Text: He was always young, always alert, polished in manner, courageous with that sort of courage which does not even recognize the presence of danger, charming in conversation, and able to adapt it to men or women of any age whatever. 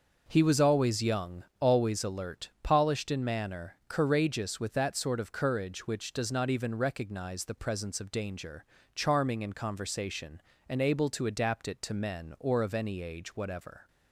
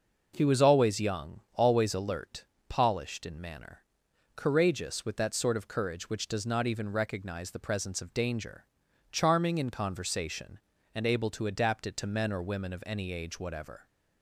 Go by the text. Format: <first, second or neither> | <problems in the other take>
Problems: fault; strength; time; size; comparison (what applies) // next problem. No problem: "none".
second | starts louder than the rest; until 1.2 s; 6 dB // skips "women"; at 12.6 s